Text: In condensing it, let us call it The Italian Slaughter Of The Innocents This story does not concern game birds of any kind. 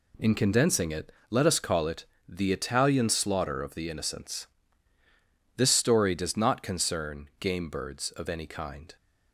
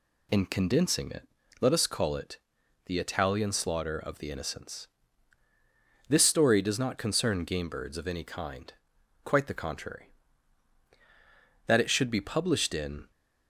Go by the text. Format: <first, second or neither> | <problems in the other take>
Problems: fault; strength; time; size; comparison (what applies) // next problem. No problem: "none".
first | pauses between "it" and "The"; noticeable; at 2.3 s; 0.48 s long; slight in the first // pauses between "Innocents" and "This"; at 4.8 s; 1.2 s long; also in the first // goes on to say "Quite the contrary That it should be published in"; strong; from 9.2 s on; 3.8 s long